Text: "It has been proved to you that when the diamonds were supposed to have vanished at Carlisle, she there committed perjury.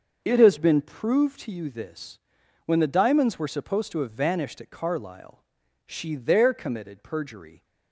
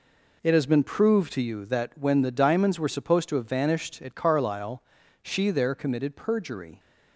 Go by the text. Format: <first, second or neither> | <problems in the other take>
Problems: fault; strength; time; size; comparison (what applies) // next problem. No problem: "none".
second | starts louder than the rest; noticeable; until 1.2 s; 6 dB // says "this" for "that"; at 1.6 s